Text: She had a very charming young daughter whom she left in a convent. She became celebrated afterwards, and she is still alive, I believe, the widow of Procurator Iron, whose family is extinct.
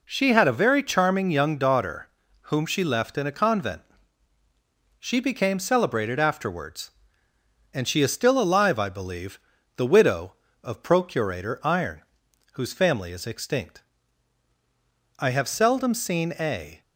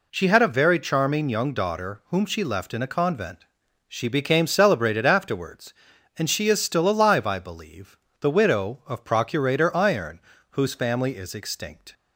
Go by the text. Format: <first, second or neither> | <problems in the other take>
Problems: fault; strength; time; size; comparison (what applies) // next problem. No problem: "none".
second | pauses between "daughter" and "whom"; at 2.0 s; 0.40 s long // goes on to say "I have seldom seen a"; from 15.1 s on; 1.6 s long